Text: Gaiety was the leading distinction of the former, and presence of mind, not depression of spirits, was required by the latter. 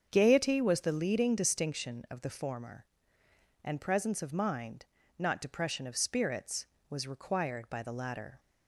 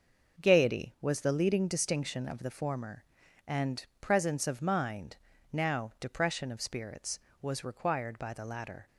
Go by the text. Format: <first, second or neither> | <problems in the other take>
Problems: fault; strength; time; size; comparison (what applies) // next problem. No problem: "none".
first | starts louder than the rest; noticeable; until 1.4 s; 6 dB; also in the first // pauses between "and" and "presence"; slight; at 3.8 s; 0.16 s long // says "now" for "not"; at 5.5 s